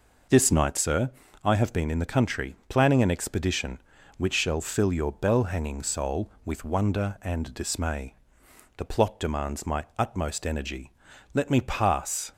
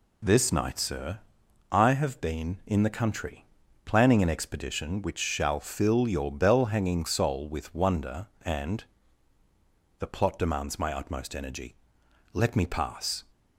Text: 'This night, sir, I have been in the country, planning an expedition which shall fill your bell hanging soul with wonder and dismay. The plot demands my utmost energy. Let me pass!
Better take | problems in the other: first | skips "dismay"; at 9.4 s

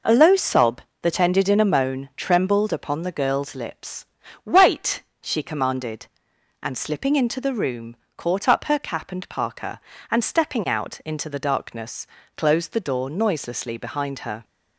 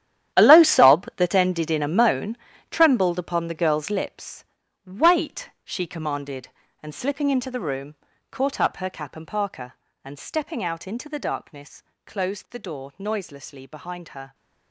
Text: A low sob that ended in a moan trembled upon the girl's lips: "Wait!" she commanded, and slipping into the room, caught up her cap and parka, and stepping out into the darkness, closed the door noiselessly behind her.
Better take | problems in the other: first | gets quieter; strong; throughout; 14.5 dB // pauses between "moan" and "trembled"; slight; at 2.3 s; 0.32 s long

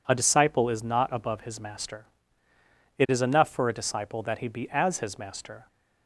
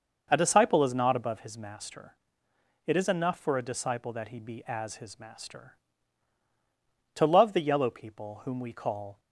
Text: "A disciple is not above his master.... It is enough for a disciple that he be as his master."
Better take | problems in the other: first | goes on to say "To love the yellow people whom we call"; strong; from 7.1 s on; 2.0 s long

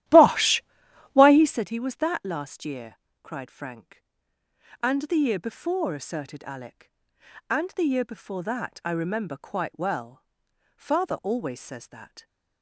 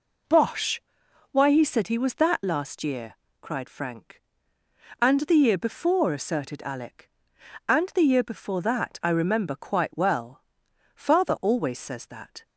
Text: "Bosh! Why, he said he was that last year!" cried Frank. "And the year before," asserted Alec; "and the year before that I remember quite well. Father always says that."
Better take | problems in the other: second | starts louder than the rest; strong; until 1.6 s; 13.5 dB

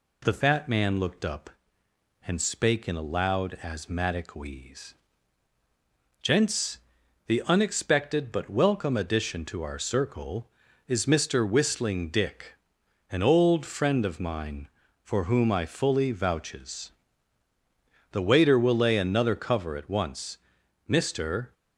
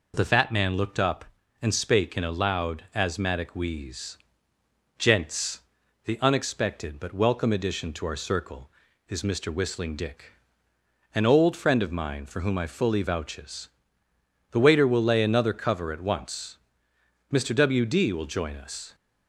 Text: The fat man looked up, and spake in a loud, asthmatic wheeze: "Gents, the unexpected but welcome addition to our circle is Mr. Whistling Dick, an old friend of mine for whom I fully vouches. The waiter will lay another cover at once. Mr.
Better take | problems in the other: first | goes on to say "W D will join us"; from 17.5 s on; 1.4 s long

